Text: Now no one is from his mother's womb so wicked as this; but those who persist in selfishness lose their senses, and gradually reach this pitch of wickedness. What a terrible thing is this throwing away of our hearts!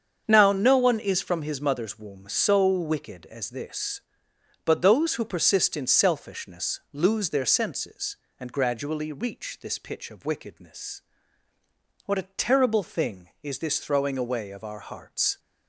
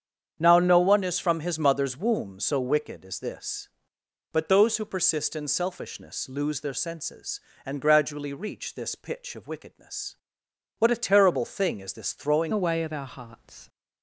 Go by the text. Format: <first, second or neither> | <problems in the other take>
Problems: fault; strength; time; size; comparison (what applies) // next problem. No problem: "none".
first | starts louder than the rest; strong; until 1.4 s; 8 dB; strong in the first // changes voice at "away"; from 12.5 s on; 1.1 s long